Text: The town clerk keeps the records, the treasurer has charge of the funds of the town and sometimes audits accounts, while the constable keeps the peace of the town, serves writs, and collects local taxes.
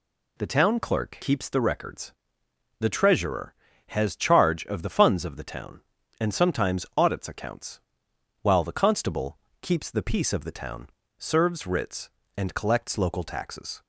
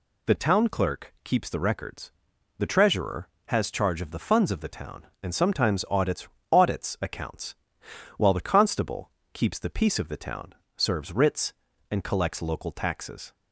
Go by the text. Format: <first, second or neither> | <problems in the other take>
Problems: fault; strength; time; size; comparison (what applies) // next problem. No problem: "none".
first | says "audits" twice; at 6.5 s // pauses between "constable" and "keeps"; slight; at 9.0 s; 0.24 s long; slight in the first